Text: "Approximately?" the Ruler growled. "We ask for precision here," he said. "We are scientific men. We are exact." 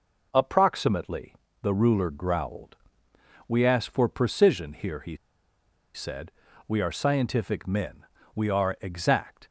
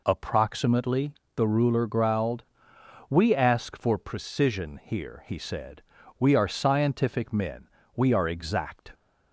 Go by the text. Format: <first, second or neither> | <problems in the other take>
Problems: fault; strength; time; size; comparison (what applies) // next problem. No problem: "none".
second | pauses between "he" and "said"; noticeable; at 5.1 s; 0.77 s long